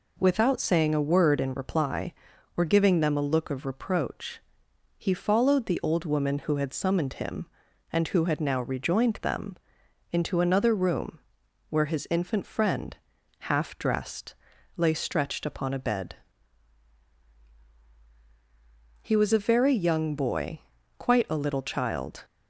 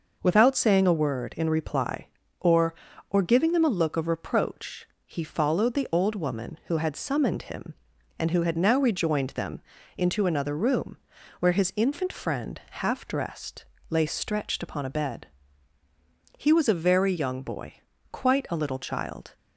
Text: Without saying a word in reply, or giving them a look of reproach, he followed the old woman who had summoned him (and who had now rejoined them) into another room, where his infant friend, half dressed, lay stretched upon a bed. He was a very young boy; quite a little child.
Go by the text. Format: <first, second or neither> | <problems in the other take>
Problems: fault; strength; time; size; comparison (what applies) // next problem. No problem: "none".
first | says "or" twice; at 3.0 s